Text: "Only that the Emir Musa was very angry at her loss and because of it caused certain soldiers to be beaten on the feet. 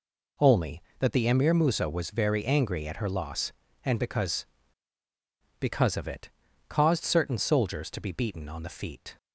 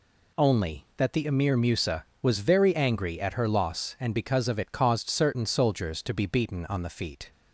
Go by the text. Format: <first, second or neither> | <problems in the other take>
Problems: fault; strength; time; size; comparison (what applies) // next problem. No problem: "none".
second | says "because" twice; at 5.5 s // pauses between "it" and "caused"; at 6.2 s; 0.40 s long